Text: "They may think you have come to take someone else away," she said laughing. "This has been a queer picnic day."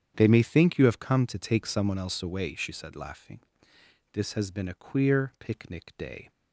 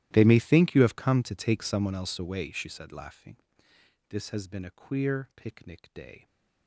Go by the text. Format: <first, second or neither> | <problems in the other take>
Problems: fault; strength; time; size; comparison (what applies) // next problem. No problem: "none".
first | gets quieter; strong; throughout; 22 dB // starts louder than the rest; strong; until 1.1 s; 14 dB; strong in the first